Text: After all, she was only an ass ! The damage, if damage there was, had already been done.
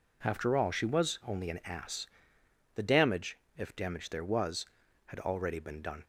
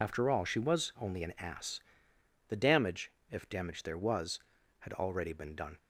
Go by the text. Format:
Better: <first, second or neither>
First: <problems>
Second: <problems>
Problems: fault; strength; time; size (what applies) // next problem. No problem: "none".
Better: first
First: none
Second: loses the start of "After"; at 0.0 s; 65 ms